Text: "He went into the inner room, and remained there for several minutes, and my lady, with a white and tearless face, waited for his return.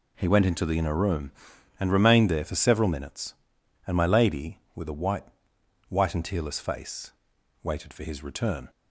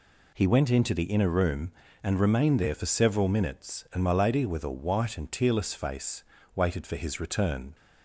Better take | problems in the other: second | says "white" twice; at 5.8 s

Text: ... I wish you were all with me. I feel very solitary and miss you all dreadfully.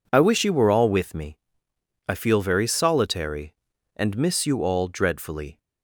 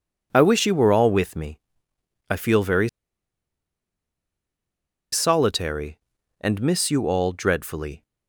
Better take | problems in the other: first | pauses between "very" and "solitary"; strong; at 2.8 s; 2.2 s long

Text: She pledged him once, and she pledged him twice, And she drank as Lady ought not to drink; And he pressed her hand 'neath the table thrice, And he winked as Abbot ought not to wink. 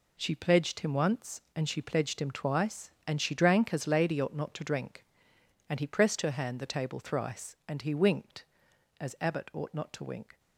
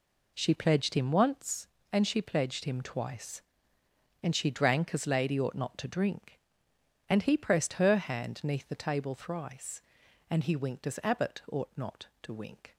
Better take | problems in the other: second | skips "neath"; at 6.5 s

